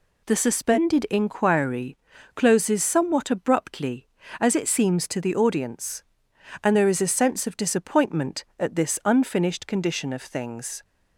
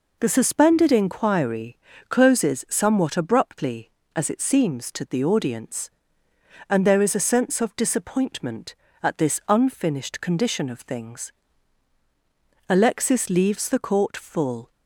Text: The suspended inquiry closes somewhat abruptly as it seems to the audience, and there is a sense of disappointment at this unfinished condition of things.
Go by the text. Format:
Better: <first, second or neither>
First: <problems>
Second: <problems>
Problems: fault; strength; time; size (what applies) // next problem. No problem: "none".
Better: first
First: pauses between "inquiry" and "closes"; at 1.9 s; 0.38 s long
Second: pauses between "inquiry" and "closes"; slight; at 1.7 s; 0.30 s long // goes on to say "Alexis leaves the court full"; strong; from 12.6 s on; 2.0 s long